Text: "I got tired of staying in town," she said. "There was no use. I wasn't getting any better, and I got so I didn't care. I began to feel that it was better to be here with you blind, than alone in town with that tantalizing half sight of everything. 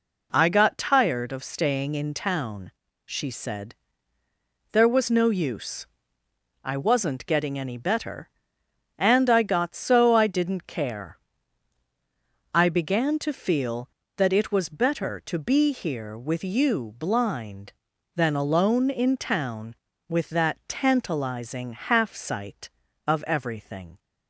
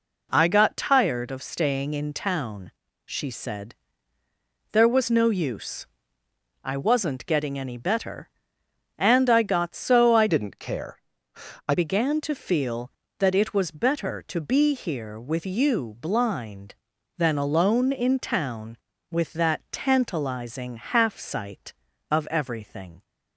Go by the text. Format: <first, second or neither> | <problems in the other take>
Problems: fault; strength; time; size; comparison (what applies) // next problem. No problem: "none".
first | changes voice from "didn't" to "I"; from 10.2 to 11.7 s; 1.5 s long